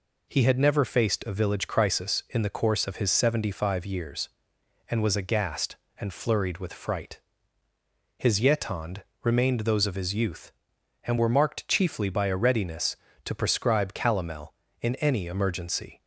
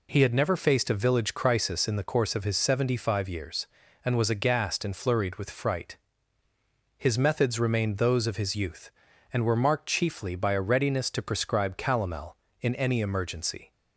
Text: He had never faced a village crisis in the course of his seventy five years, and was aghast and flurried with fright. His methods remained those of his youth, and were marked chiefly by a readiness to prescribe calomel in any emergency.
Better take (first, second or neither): second